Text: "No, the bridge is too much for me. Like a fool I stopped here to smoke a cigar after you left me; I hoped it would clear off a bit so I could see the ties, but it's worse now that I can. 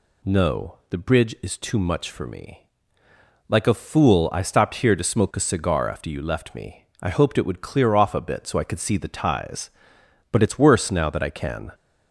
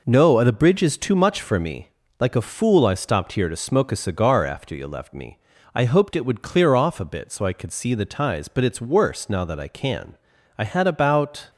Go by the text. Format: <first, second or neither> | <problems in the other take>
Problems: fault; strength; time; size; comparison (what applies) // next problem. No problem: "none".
first | goes on to say "I had about"; noticeable; from 10.5 s on; 0.92 s long